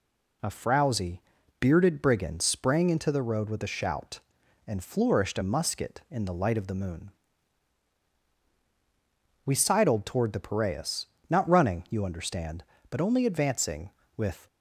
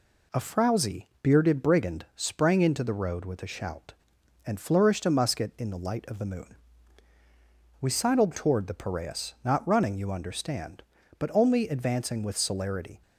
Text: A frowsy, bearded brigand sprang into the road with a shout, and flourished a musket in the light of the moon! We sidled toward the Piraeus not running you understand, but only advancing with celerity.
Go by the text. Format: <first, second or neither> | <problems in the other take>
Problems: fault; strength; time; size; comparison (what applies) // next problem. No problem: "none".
second | pauses between "Piraeus" and "not"; slight; at 11.0 s; 0.20 s long // stops before "celerity"; at 14.4 s